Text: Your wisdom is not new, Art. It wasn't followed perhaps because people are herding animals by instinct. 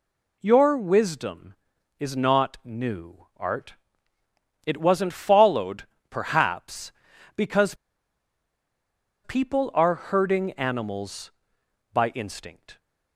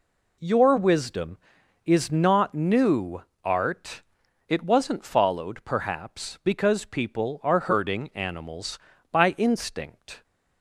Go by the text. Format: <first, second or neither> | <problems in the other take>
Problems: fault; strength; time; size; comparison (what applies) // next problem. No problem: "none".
second | pauses between "followed" and "perhaps"; slight; at 5.8 s; 0.26 s long // pauses between "because" and "people"; strong; at 7.7 s; 1.4 s long